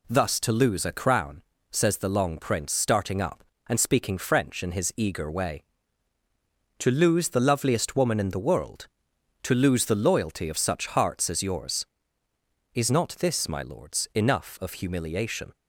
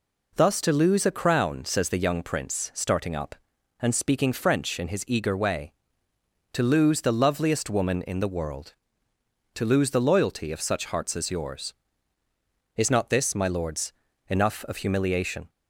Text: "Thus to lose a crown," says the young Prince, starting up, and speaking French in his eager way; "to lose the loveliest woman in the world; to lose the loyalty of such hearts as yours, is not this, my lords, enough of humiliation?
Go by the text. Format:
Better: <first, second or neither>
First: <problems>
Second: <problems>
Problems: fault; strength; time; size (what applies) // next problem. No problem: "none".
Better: second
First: says "long" for "young"; at 2.0 s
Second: none